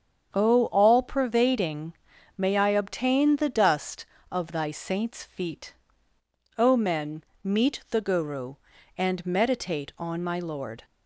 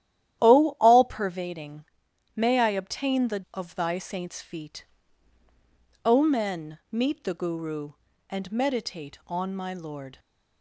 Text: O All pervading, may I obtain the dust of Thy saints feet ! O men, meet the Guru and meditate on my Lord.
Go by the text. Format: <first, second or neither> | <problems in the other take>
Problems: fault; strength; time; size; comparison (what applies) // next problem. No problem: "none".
first | starts louder than the rest; strong; until 1.4 s; 11.5 dB; strong in the first // skips "dust"; at 3.4 s